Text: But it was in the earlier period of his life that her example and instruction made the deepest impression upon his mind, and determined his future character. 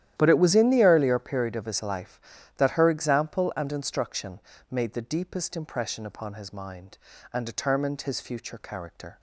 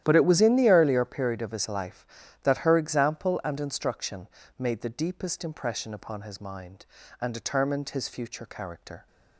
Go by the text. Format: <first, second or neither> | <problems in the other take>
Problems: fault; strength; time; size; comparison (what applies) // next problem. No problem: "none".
neither | starts louder than the rest; strong; the same in both // pauses between "instruction" and "made"; slight; the same in both